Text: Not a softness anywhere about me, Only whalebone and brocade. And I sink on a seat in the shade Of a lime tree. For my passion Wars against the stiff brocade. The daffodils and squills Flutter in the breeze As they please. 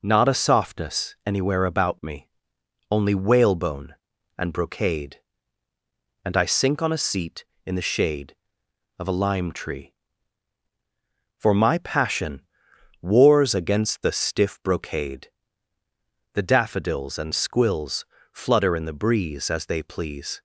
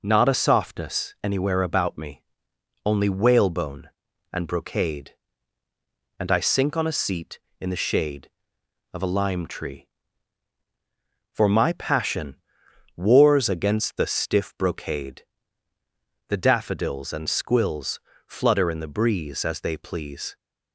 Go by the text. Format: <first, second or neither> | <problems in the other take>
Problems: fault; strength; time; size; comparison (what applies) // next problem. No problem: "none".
neither | pauses between "passion" and "Wars"; noticeable; the same in both // pauses between "squills" and "Flutter"; slight; the same in both